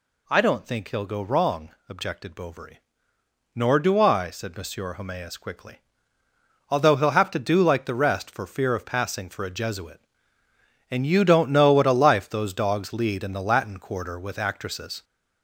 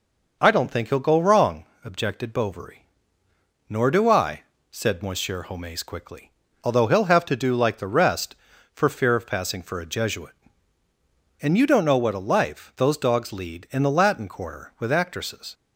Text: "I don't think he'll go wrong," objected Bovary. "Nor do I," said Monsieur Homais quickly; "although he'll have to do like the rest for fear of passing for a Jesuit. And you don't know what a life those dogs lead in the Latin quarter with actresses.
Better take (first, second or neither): second